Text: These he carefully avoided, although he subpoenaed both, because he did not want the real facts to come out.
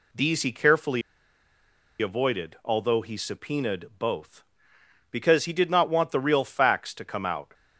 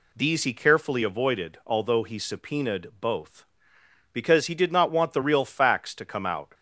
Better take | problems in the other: second | pauses between "carefully" and "avoided"; at 1.0 s; 0.99 s long

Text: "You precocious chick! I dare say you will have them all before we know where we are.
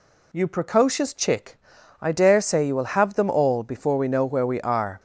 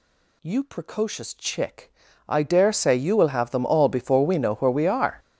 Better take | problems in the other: first | gets louder; strong; throughout; 17.5 dB

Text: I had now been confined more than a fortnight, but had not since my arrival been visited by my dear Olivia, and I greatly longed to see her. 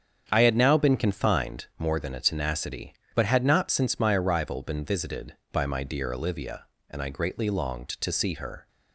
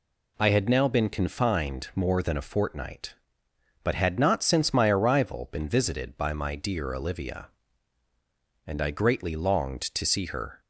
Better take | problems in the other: second | starts louder than the rest; strong; until 1.3 s; 8 dB // says "tenacity" for "fortnight"; at 2.1 s

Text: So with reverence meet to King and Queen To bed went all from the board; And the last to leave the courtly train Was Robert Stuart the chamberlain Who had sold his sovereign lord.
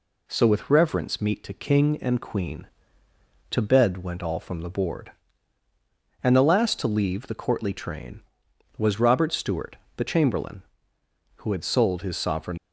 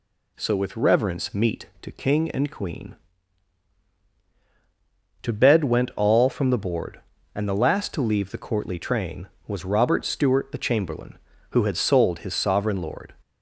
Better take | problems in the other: second | pauses between "Stuart" and "the"; slight; at 9.7 s; 0.20 s long // stops before "lord"; at 12.5 s

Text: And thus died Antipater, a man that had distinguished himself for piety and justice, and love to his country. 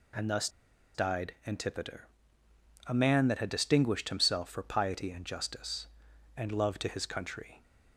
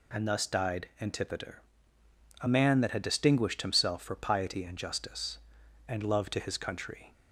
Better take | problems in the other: second | pauses between "thus" and "died"; noticeable; at 0.4 s; 0.46 s long

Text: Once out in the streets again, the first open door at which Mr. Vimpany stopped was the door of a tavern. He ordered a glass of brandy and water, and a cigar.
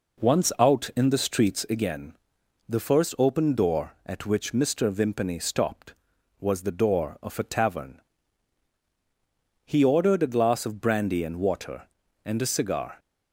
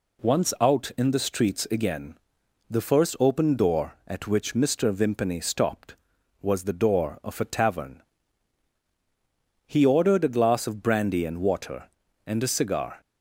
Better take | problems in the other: second | starts louder than the rest; noticeable; until 1.6 s; 4 dB

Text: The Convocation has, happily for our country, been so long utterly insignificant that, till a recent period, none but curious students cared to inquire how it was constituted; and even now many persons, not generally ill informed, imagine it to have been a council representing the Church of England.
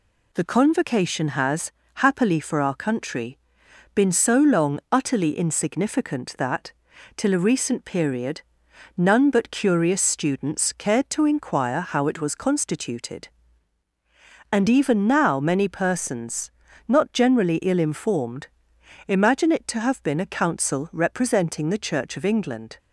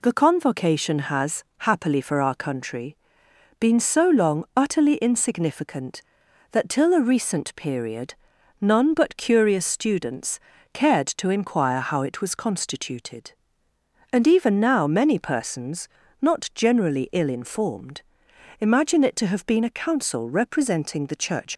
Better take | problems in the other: first | pauses between "students" and "cared"; slight; at 10.3 s; 0.34 s long // stops before "of England"; at 21.5 s

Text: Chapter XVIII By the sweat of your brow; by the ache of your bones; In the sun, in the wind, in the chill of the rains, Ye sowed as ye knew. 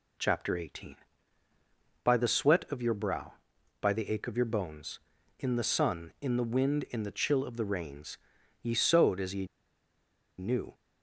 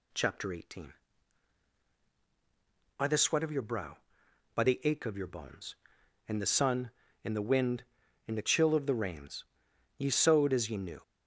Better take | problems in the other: second | pauses between "ye" and "knew"; noticeable; at 9.4 s; 0.93 s long

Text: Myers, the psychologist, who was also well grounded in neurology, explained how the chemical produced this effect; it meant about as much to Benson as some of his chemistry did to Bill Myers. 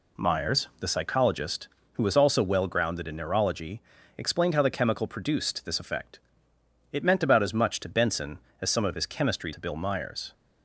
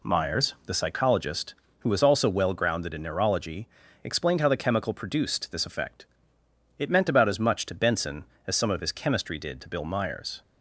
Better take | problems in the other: second | skips "did"; at 9.5 s

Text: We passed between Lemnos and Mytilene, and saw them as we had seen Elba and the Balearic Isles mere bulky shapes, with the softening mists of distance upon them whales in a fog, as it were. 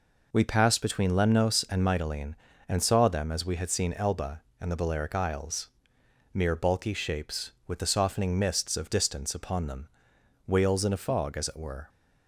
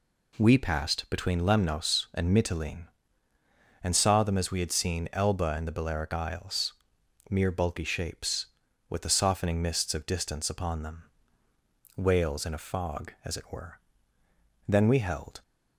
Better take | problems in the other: first | pauses between "Isles" and "mere"; noticeable; at 6.7 s; 0.58 s long; noticeable in the first // pauses between "them" and "whales"; noticeable; at 11.0 s; 0.94 s long; noticeable in the first // goes on to say "Then we held"; noticeable; from 14.6 s on; 0.76 s long

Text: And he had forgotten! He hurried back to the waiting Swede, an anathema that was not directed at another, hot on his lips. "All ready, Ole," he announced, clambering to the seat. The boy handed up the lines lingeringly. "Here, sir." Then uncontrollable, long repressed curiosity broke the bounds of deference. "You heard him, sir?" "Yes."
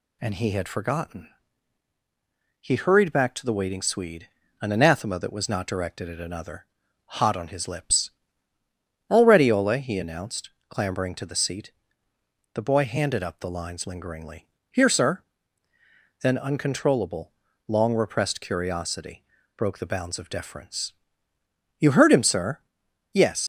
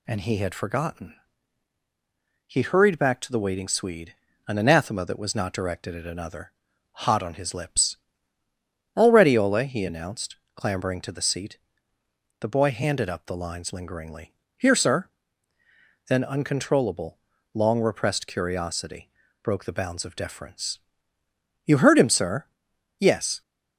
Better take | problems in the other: second | pauses between "curiosity" and "broke"; slight; at 19.2 s; 0.32 s long; slight in the second // leaves "Yes" unfinished; at 23.4 s; 80 ms

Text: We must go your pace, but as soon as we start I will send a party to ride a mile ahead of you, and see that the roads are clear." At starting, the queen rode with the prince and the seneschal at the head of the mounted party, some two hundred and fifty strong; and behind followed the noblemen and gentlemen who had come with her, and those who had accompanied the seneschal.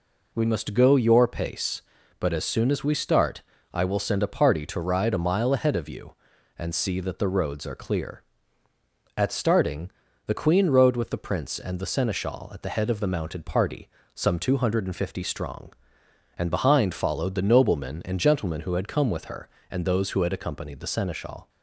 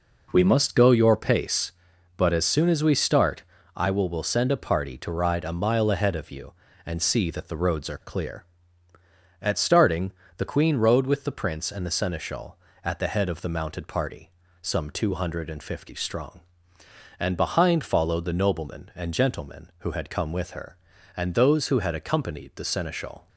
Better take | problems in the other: first | pauses between "start" and "I"; slight; at 3.4 s; 0.32 s long; slight in the first // says "will" twice; at 4.0 s

